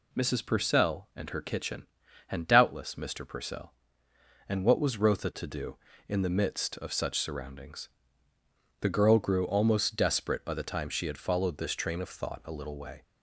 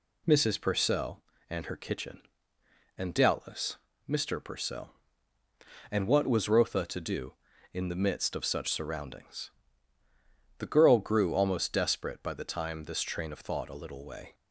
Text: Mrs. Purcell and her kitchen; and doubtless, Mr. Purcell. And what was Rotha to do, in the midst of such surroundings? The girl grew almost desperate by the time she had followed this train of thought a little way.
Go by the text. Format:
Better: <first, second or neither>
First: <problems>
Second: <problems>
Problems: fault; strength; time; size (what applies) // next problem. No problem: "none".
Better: first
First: none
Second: skips "she had followed"; at 12.8 s